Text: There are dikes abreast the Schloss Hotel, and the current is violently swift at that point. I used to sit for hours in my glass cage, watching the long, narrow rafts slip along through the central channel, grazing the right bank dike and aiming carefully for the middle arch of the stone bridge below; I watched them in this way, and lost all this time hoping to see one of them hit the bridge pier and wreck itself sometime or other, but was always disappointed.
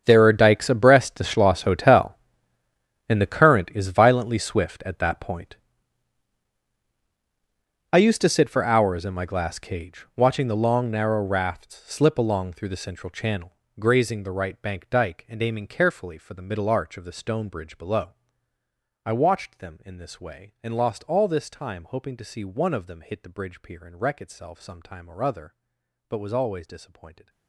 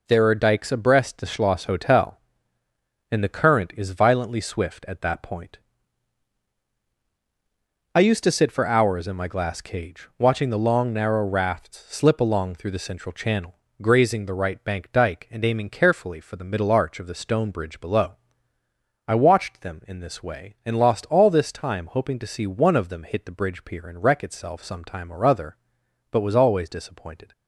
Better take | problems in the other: second | gets quieter; strong; throughout; 18.5 dB

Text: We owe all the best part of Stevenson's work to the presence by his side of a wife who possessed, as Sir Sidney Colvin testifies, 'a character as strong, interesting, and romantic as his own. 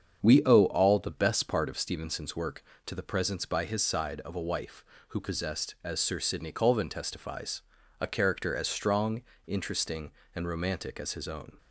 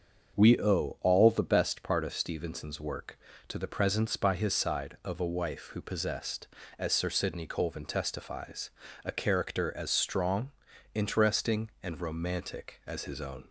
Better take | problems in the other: neither | starts louder than the rest; the same in both

